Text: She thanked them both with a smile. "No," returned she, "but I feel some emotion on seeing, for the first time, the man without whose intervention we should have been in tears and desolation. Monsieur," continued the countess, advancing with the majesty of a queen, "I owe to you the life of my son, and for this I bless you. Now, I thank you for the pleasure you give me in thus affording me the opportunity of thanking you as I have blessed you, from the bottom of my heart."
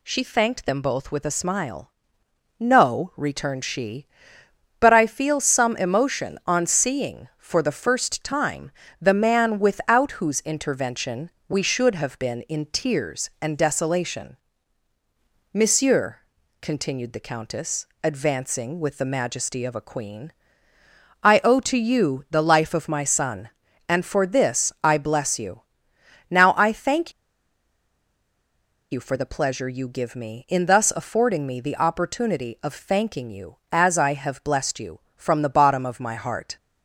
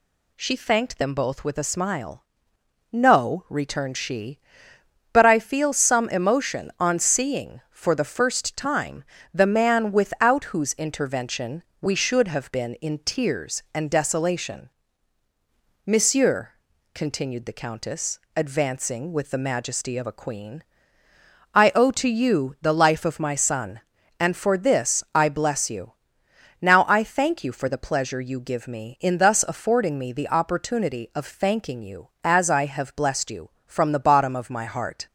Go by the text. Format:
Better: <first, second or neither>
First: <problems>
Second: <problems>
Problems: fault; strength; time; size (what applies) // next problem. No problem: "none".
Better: second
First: pauses between "intervention" and "we"; slight; at 11.3 s; 0.16 s long // pauses between "thank" and "you"; strong; at 27.1 s; 1.8 s long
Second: pauses between "intervention" and "we"; slight; at 11.6 s; 0.16 s long